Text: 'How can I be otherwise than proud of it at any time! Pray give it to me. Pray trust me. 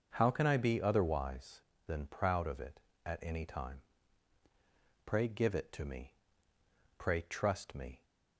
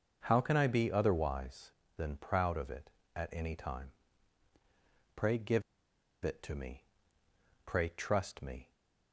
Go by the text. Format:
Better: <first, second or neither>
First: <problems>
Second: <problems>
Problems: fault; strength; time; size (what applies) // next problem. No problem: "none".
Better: first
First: starts louder than the rest; noticeable; until 1.1 s; 6 dB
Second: starts louder than the rest; noticeable; until 1.2 s; 6 dB // pauses between "give" and "it"; noticeable; at 5.6 s; 0.61 s long